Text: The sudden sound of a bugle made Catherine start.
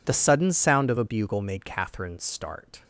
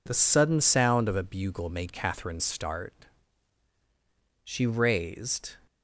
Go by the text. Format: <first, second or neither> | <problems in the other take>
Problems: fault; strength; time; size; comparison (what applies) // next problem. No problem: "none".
first | goes on to say "She raised"; noticeable; from 4.4 s on; 1.1 s long